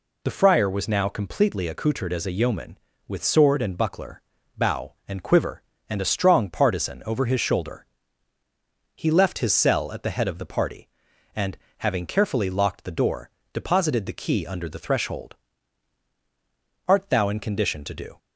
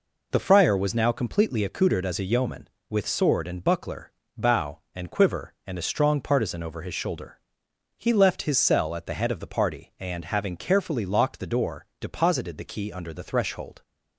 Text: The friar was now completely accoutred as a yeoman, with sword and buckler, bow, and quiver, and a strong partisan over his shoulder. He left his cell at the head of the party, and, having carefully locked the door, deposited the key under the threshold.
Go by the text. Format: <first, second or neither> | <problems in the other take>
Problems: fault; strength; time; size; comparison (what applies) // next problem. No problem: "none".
second | goes on to say "Art thou in condition to do"; from 16.8 s on; 1.3 s long